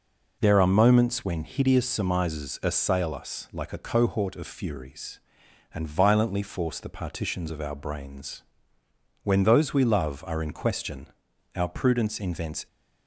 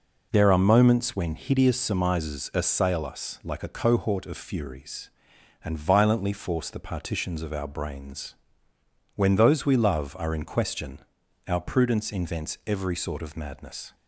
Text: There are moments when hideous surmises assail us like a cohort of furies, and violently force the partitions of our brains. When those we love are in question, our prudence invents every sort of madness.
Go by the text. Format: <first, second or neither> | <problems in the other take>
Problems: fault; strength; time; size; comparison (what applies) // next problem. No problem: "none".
second | stops before "every sort of madness"; at 12.6 s